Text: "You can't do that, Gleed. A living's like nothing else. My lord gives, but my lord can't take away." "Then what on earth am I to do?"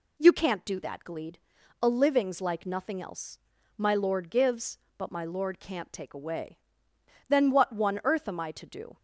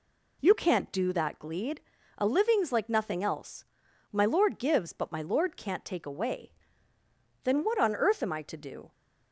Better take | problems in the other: second | says "one" for "on"; at 7.7 s

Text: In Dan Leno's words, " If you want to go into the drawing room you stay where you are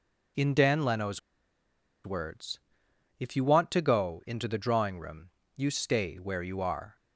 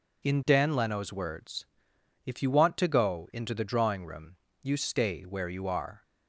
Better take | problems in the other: second | pauses between "Leno's" and "words"; noticeable; at 1.1 s; 0.85 s long // pauses between "room" and "you"; slight; at 5.3 s; 0.26 s long; slight in the second

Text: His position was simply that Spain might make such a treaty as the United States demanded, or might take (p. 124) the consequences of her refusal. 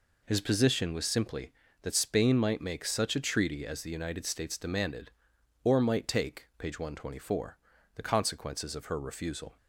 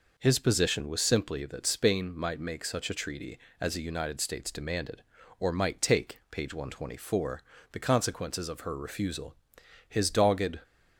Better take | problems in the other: first | goes on to say "His dogged"; noticeable; from 9.8 s on; 0.70 s long

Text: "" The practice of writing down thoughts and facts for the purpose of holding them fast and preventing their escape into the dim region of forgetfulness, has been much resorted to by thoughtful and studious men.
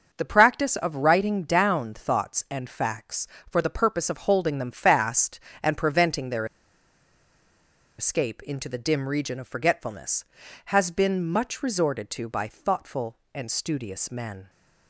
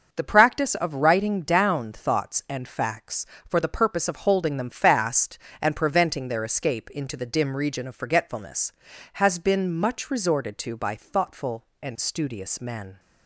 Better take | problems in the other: second | starts louder than the rest; until 1.1 s; 6.5 dB; also in the second // pauses between "their" and "escape"; strong; at 6.4 s; 1.5 s long

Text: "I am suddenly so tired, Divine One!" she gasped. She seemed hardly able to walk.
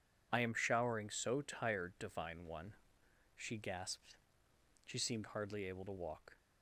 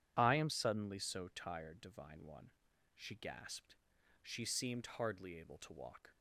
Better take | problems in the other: second | says "showering" for "suddenly"; at 0.5 s

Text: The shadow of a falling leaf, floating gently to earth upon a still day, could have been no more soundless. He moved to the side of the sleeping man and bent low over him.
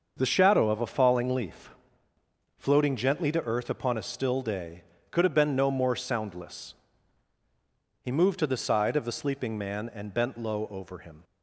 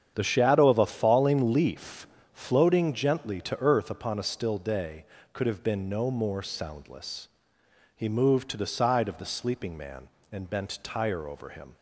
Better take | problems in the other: first | starts louder than the rest; strong; until 1.1 s; 8 dB; also in the first // says "tire" for "low"; at 10.8 s

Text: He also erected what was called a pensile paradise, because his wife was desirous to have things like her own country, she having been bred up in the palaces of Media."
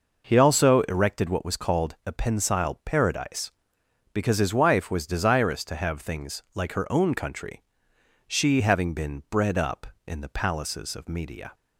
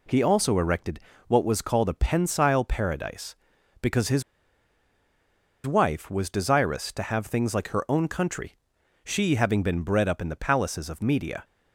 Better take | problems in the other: first | pauses between "erected" and "what"; slight; at 0.9 s; 0.28 s long // pauses between "his" and "wife"; strong; at 4.2 s; 1.4 s long

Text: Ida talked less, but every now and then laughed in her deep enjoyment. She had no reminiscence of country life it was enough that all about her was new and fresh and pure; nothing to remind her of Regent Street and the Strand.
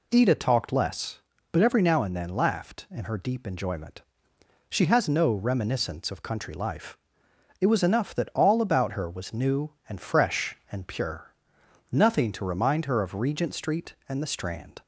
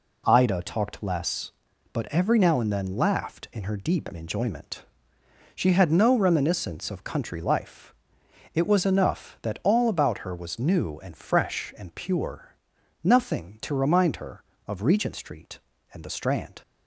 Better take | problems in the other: second | says "has" for "had"; at 4.8 s // pauses between "life" and "it"; noticeable; at 6.9 s; 0.64 s long; noticeable in the second

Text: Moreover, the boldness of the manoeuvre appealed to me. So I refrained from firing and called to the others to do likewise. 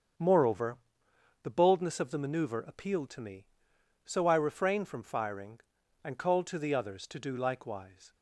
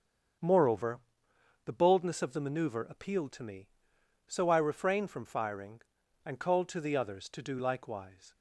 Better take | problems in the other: neither | starts louder than the rest; strong; the same in both

